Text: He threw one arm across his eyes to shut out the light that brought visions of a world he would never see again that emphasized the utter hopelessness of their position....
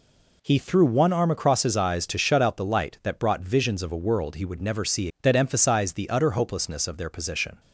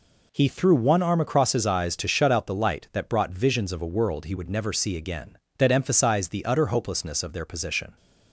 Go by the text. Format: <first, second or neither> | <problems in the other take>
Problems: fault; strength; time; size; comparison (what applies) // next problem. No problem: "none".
second | skips "again"; at 5.1 s